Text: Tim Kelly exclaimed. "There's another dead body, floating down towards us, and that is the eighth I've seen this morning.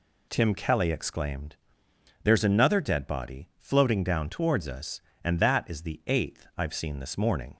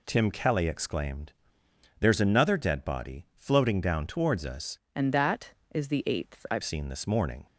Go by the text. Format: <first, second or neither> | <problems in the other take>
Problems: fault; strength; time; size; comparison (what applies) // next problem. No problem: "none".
first | changes voice from "and" to "I've"; from 4.9 to 6.6 s; 1.7 s long